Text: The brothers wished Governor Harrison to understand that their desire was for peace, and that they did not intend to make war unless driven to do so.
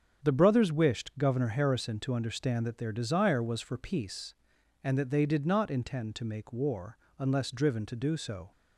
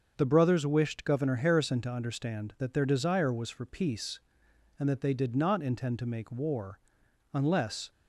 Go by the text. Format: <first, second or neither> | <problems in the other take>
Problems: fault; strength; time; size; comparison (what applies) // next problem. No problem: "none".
first | starts louder than the rest; until 1.1 s; 6.5 dB; strong in the first // pauses between "war" and "unless"; noticeable; at 6.7 s; 0.54 s long; slight in the first // stops before "driven to do so"; at 7.9 s